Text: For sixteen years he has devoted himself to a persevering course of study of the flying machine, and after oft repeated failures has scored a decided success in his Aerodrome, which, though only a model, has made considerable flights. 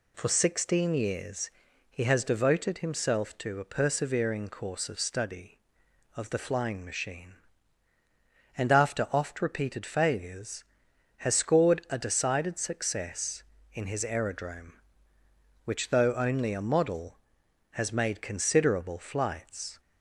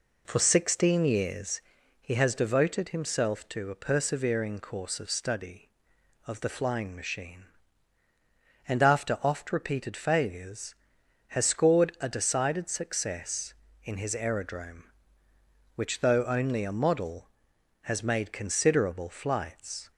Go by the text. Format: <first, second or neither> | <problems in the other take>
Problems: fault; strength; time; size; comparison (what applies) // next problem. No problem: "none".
first | starts louder than the rest; until 1.6 s; 3.5 dB // pauses between "years" and "he"; at 1.6 s; 0.42 s long; also in the first